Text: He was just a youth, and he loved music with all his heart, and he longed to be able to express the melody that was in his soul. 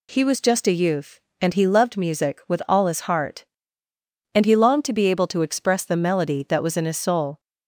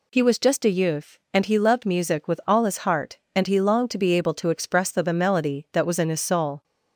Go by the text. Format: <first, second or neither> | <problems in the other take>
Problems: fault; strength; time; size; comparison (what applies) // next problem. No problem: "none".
first | says "the" twice; at 5.0 s